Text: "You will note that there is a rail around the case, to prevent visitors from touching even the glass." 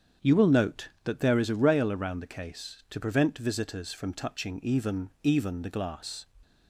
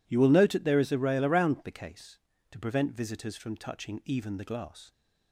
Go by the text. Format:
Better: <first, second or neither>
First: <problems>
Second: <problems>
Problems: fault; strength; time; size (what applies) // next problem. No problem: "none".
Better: second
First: starts louder than the rest; strong; until 1.3 s; 7.5 dB // says "even" twice; at 5.2 s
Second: none